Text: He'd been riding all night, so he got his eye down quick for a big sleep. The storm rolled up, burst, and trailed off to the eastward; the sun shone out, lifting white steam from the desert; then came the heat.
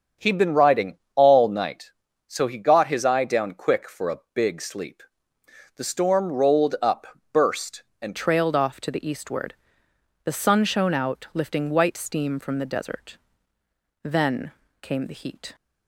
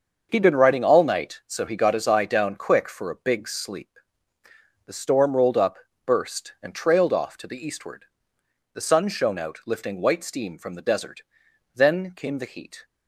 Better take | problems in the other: second | starts louder than the rest; until 1.3 s; 7 dB; also in the second // pauses between "riding" and "all"; slight; at 0.9 s; 0.18 s long // changes voice at "trailed"; from 8.1 s on; 7.4 s long // pauses between "then" and "came"; slight; at 14.5 s; 0.30 s long

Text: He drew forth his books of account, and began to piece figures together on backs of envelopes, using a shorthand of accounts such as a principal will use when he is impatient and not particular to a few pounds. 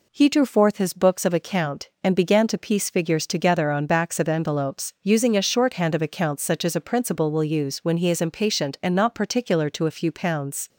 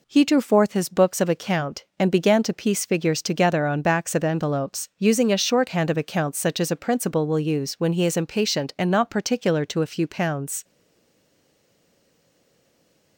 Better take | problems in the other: first | stays silent after the last word; strong; from 10.6 s on; 2.5 s long

